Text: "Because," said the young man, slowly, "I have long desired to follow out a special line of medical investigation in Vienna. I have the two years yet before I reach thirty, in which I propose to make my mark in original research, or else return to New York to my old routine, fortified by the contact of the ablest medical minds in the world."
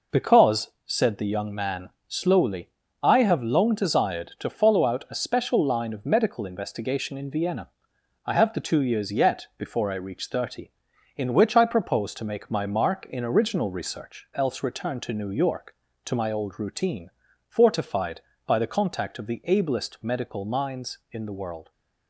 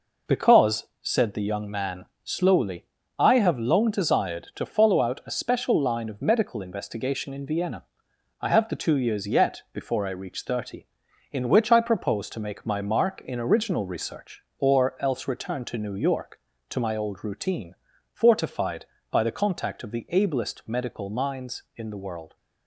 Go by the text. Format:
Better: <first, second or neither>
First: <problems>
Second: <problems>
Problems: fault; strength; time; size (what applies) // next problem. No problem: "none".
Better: second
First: skips "or"; at 14.3 s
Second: none